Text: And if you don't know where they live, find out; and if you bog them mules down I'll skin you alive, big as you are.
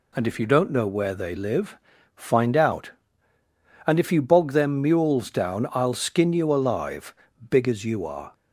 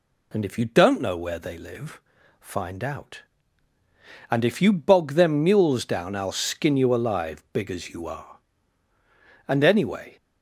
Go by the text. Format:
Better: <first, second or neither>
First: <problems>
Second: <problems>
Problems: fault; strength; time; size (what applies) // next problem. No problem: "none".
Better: first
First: none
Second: goes on to say "And anyway"; noticeable; from 9.4 s on; 0.70 s long